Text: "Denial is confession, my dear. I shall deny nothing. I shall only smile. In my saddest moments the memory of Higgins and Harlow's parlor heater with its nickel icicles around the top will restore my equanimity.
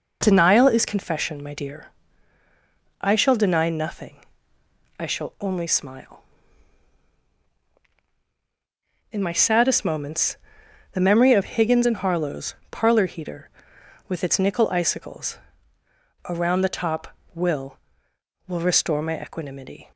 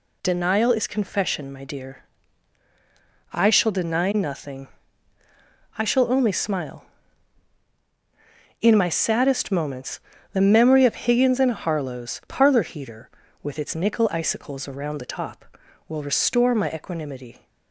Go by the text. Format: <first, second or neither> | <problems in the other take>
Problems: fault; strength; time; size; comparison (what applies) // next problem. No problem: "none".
second | pauses between "moments" and "the"; noticeable; at 10.3 s; 0.56 s long; slight in the second // pauses between "Harlow's" and "parlor"; slight; at 12.5 s; 0.16 s long // pauses between "icicles" and "around"; noticeable; at 15.3 s; 0.90 s long // says "will" twice; at 18.4 s